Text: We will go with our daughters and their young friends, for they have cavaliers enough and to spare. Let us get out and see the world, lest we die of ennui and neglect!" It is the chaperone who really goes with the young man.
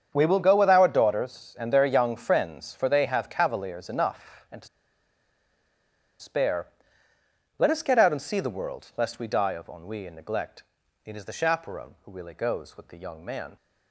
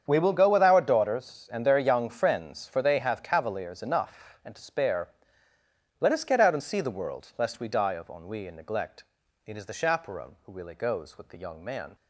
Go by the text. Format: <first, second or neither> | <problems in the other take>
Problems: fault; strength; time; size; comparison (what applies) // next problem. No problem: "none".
second | starts louder than the rest; strong; until 1.1 s; 7.5 dB; strong in the second // pauses between "to" and "spare"; strong; at 4.6 s; 1.5 s long